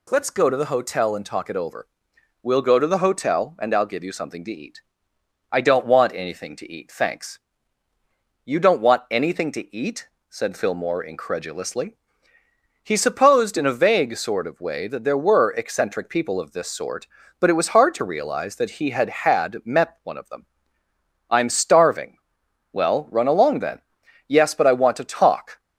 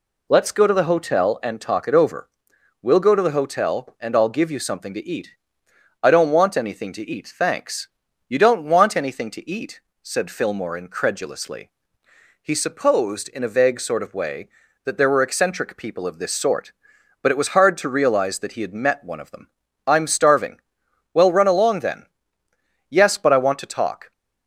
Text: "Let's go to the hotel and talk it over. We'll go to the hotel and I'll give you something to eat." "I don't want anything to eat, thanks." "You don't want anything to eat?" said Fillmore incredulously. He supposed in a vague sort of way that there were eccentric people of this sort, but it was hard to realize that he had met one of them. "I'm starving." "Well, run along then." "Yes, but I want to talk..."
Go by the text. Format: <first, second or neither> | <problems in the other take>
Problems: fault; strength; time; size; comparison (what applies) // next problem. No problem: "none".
second | says "had" twice; at 19.1 s